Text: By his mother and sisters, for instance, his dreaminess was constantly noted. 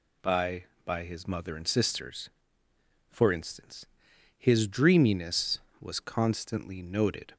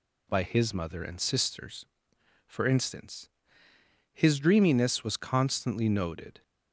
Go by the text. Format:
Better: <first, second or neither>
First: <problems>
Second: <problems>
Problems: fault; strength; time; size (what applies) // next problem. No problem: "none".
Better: second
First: says "By" twice; at 0.8 s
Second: none